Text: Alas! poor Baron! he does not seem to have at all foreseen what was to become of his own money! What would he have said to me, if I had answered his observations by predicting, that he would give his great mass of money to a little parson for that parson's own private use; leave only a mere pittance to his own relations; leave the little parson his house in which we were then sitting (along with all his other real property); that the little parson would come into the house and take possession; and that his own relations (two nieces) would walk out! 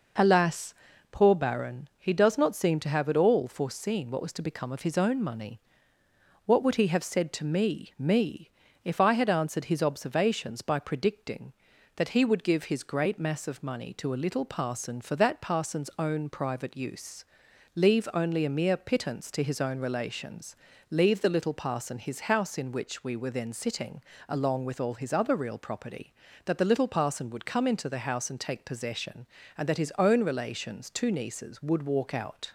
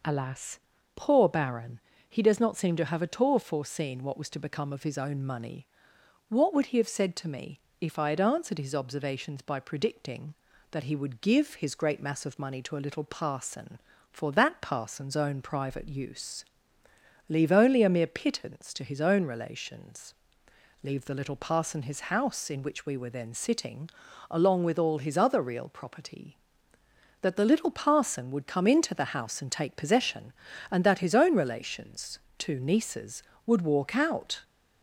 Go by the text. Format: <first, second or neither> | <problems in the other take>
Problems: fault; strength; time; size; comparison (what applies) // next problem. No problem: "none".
second | says "me" twice; at 7.9 s